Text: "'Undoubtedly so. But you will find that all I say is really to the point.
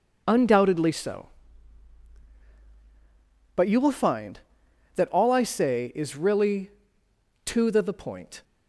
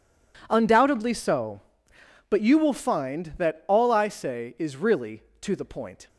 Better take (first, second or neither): second